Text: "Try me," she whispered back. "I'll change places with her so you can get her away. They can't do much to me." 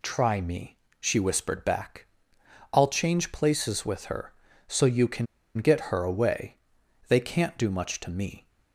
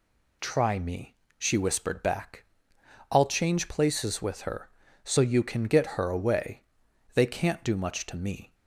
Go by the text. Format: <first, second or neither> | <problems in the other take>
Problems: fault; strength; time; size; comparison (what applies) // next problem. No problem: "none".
second | pauses between "can" and "get"; slight; at 5.2 s; 0.31 s long